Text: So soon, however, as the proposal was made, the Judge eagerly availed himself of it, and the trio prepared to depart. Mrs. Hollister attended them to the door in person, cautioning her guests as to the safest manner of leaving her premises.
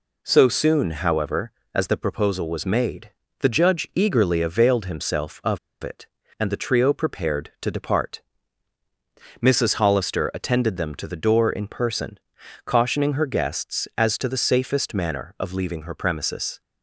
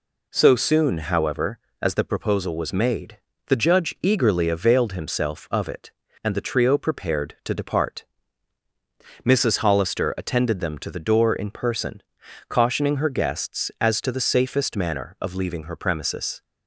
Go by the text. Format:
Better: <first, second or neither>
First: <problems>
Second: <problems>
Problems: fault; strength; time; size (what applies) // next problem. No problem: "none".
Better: second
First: pauses between "of" and "it"; slight; at 5.5 s; 0.25 s long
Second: none